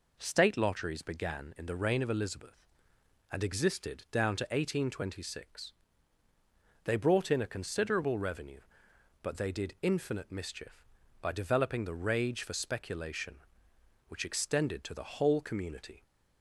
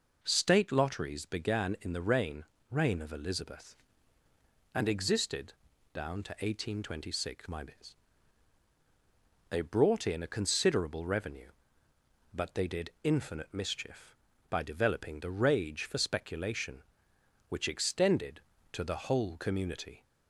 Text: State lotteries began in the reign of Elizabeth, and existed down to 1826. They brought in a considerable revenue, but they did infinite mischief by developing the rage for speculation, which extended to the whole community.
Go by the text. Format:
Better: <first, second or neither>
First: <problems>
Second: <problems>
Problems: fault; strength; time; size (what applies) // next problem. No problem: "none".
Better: first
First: none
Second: says "reign" twice; at 2.6 s // pauses between "existed" and "down"; at 5.5 s; 0.40 s long